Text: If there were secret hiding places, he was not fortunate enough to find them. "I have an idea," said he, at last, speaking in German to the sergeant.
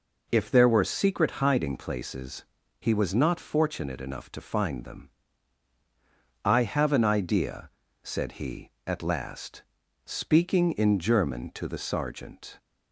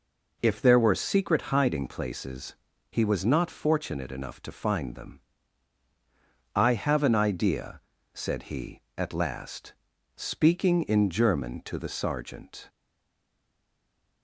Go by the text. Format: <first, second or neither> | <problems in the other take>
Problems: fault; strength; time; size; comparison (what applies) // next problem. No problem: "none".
first | stays silent after the last word; noticeable; from 12.6 s on; 1.6 s long